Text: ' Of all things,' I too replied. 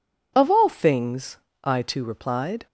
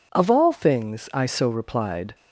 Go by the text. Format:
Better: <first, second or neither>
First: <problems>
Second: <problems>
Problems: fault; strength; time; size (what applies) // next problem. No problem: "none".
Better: first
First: none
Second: says "so" for "too"; at 1.2 s